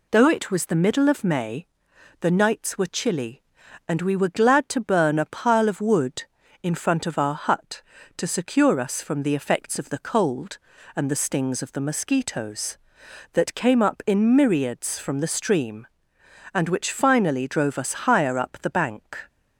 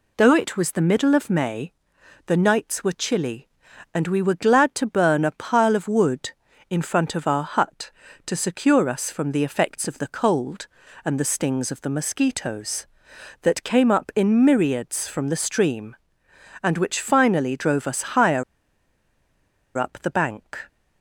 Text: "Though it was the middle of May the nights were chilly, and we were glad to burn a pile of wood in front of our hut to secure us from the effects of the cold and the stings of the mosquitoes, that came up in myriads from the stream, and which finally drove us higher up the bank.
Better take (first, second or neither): first